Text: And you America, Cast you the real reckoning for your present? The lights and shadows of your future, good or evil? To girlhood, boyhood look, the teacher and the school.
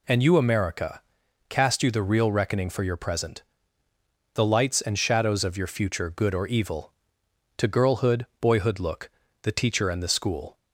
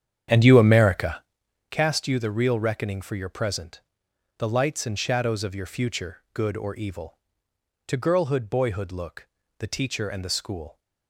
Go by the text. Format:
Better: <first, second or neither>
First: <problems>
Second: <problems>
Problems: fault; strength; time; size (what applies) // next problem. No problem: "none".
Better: first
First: none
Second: starts louder than the rest; strong; until 1.3 s; 9 dB